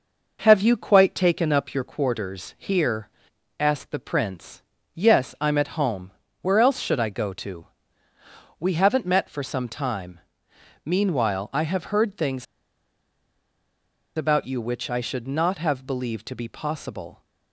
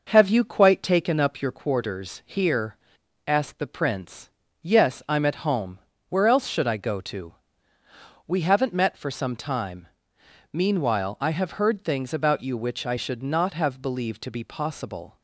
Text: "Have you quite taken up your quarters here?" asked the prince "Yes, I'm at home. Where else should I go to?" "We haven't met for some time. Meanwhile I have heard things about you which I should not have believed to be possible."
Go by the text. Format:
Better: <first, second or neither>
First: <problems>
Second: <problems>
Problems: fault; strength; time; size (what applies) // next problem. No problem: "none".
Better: second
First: pauses between "prince" and "Yes"; slight; at 4.6 s; 0.32 s long // pauses between "things" and "about"; strong; at 12.4 s; 1.7 s long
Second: pauses between "prince" and "Yes"; slight; at 4.2 s; 0.32 s long